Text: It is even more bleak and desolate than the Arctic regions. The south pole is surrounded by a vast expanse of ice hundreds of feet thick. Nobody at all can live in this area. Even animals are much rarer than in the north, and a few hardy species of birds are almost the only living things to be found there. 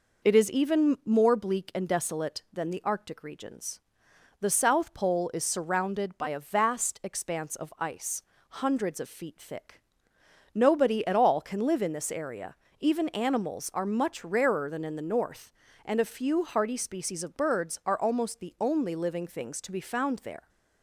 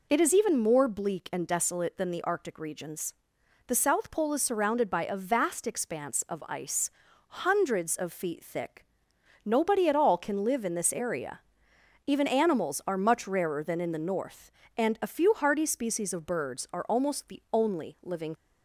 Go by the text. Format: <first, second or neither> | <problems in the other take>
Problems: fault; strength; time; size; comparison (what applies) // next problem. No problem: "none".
first | pauses between "ice" and "hundreds"; noticeable; at 6.9 s; 0.48 s long; slight in the first // stops before "things to be found there"; at 18.3 s